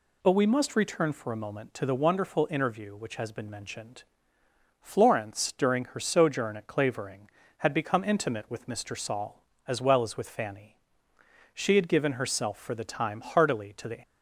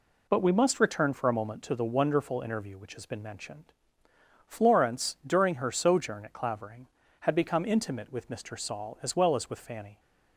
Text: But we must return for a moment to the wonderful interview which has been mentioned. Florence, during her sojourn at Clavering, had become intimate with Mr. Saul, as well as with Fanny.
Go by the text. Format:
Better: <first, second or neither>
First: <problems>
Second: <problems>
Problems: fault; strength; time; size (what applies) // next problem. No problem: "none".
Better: second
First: goes on to say "She had given herself for the time heartily to the"; strong; from 11.5 s on; 2.4 s long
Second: none